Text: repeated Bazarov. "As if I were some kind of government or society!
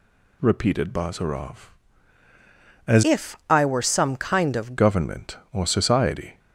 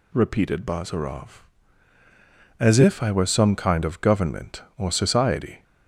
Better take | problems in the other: second | changes voice from "if" to "of"; from 3.0 to 4.7 s; 1.7 s long

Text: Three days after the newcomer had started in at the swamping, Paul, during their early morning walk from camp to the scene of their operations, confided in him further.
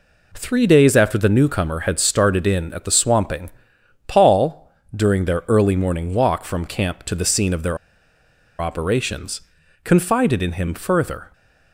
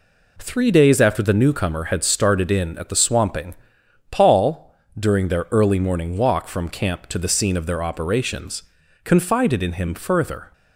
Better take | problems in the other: second | pauses between "their" and "operations"; noticeable; at 7.7 s; 0.82 s long

